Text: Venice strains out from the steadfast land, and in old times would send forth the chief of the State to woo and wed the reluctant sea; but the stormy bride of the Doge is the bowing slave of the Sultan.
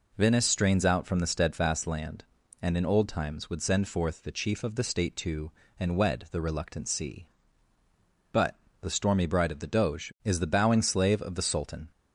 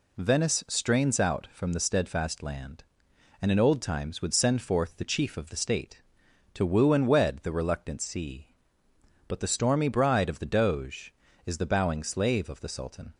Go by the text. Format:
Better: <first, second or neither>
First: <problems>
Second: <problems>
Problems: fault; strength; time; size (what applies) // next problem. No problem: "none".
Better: second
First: skips "woo"; at 5.6 s // pauses between "but" and "the"; slight; at 8.5 s; 0.26 s long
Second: none